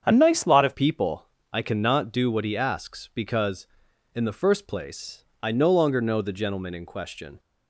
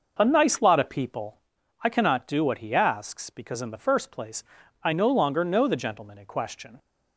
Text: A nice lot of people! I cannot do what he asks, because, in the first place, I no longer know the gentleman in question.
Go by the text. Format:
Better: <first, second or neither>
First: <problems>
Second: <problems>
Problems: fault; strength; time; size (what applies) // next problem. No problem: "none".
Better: second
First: starts louder than the rest; strong; until 1.0 s; 8 dB // changes voice at "people"; from 0.7 s on; 6.6 s long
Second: none